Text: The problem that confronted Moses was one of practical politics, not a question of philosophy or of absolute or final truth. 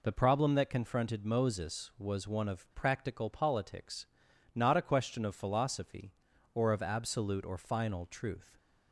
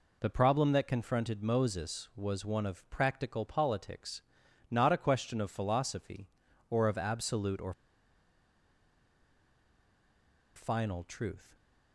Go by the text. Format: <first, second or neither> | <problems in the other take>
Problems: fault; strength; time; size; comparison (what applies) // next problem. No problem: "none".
first | pauses between "or" and "final"; strong; at 7.7 s; 2.8 s long